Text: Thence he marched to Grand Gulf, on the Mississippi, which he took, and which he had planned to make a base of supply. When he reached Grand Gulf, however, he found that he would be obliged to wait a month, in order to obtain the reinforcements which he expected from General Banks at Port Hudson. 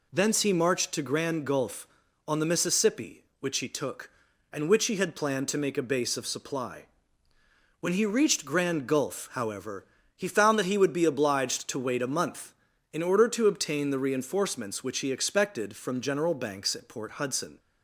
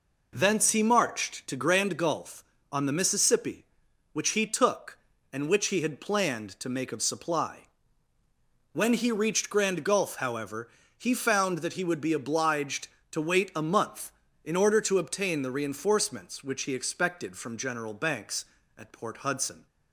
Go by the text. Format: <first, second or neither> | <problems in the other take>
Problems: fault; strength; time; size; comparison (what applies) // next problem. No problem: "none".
first | skips "a base"; at 6.9 s